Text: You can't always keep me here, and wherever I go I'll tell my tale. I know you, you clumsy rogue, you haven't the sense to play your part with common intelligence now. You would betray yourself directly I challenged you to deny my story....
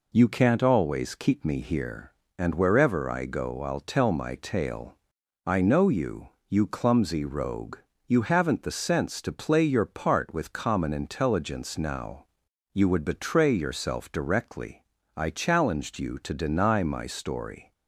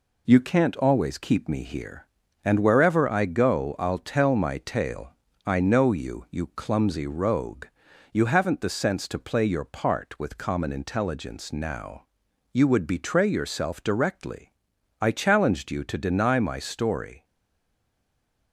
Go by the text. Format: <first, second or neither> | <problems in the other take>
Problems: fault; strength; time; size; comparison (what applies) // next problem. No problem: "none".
first | pauses between "directly" and "I"; noticeable; at 14.5 s; 0.50 s long; slight in the first // stays silent after the last word; noticeable; from 17.2 s on; 1.3 s long